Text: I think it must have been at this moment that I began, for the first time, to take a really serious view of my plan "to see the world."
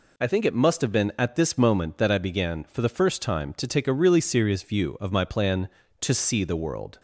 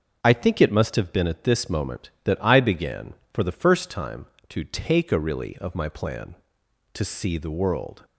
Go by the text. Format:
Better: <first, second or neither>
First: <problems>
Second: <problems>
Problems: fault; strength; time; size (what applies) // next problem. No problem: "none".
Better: first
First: none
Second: starts louder than the rest; until 1.2 s; 6.5 dB // skips "serious view"; at 5.5 s